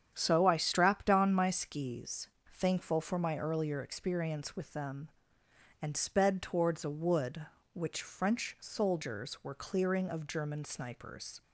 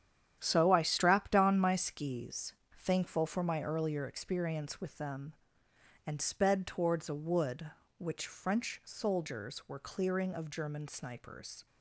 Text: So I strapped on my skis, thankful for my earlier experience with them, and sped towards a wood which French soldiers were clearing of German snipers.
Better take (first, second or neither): first